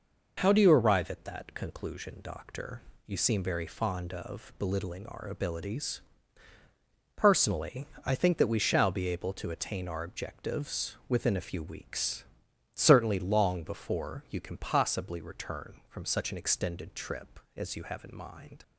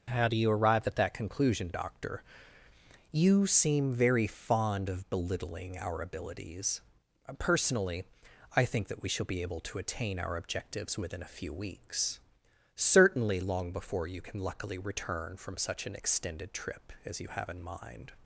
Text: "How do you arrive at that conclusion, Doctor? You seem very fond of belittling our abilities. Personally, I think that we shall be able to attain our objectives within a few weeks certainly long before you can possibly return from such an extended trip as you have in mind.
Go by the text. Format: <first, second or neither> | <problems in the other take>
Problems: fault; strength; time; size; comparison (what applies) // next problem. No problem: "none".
first | pauses between "weeks" and "certainly"; noticeable; at 12.2 s; 0.54 s long; noticeable in the first // says "luckily" for "possibly"; at 14.3 s